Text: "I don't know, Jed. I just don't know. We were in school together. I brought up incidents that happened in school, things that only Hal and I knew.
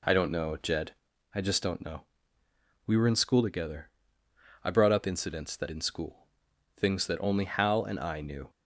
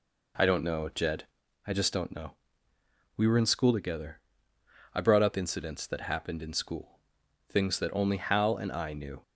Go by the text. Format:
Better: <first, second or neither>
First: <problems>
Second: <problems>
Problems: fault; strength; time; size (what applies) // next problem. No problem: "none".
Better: second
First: skips "happened"; at 5.6 s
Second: none